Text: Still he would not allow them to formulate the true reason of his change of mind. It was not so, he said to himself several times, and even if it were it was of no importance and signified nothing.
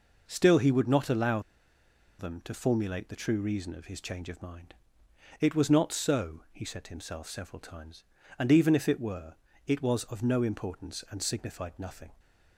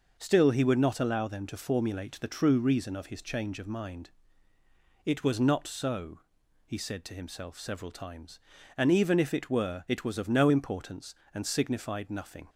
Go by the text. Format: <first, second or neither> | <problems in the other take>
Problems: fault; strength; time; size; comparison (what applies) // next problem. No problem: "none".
second | pauses between "allow" and "them"; noticeable; at 1.3 s; 0.79 s long // pauses between "were" and "it"; slight; at 9.3 s; 0.30 s long